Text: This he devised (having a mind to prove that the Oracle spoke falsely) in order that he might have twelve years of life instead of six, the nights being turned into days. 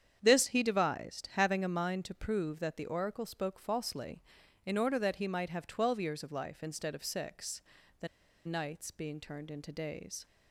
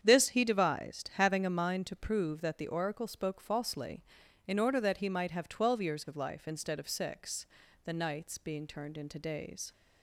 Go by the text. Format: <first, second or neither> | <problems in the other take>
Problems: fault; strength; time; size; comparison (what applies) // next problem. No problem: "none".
second | starts louder than the rest; strong; until 1.2 s; 8.5 dB; strong in the second // pauses between "the" and "nights"; at 8.0 s; 0.37 s long